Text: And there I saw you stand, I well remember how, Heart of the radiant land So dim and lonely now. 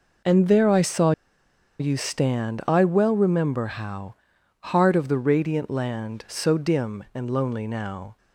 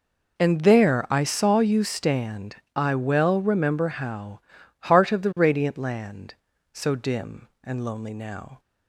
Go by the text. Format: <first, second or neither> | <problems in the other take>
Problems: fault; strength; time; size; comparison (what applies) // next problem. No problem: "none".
second | pauses between "saw" and "you"; noticeable; at 1.1 s; 0.67 s long